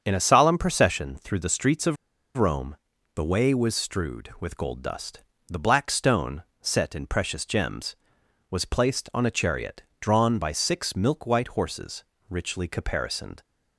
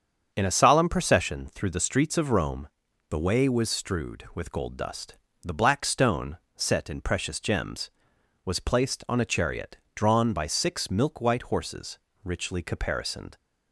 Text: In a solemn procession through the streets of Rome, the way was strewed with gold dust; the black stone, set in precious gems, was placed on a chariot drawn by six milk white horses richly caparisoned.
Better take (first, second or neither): second